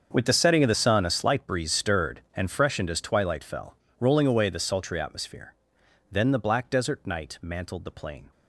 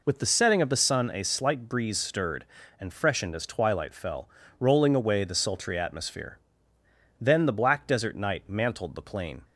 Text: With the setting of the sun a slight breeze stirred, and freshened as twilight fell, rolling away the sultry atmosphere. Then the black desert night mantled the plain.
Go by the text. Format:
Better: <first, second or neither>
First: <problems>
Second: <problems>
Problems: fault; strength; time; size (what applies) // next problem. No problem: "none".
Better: second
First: gets quieter; strong; throughout; 18 dB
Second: none